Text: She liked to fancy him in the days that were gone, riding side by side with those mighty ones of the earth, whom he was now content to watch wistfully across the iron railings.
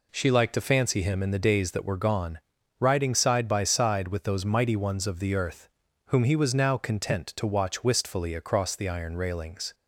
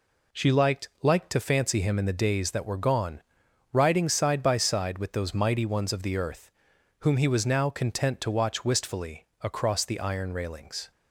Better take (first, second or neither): first